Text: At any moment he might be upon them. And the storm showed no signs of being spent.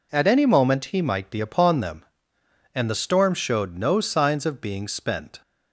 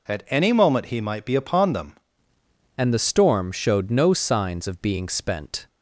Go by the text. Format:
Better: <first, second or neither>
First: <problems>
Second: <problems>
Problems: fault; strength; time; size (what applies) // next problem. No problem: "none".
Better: first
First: none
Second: changes voice at "And"; from 2.7 s on; 2.9 s long